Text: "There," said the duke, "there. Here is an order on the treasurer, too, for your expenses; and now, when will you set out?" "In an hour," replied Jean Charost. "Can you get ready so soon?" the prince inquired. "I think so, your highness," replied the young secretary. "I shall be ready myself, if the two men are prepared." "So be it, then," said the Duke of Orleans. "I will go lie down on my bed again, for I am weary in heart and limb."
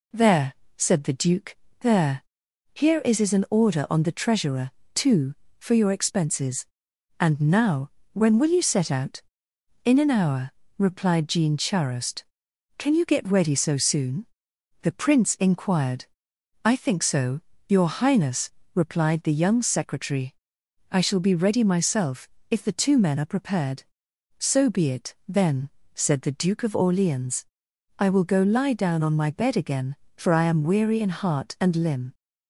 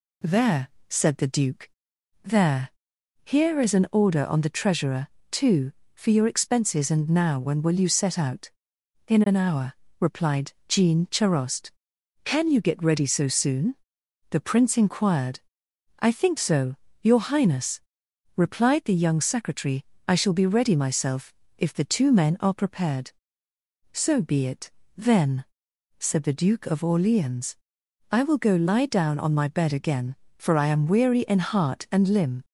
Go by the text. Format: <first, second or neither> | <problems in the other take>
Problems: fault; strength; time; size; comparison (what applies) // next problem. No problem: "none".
second | says "is" twice; at 3.2 s